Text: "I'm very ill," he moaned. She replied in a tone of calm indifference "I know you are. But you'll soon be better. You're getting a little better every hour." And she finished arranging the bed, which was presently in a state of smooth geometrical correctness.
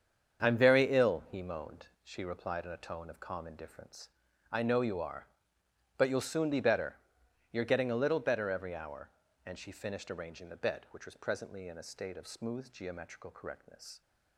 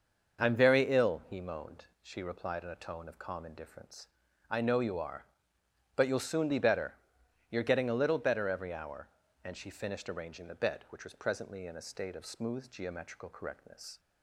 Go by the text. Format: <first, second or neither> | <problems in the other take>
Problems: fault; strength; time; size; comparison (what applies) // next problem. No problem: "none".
second | gets quieter; strong; throughout; 10.5 dB // pauses between "indifference" and "I"; at 4.0 s; 0.42 s long; also in the second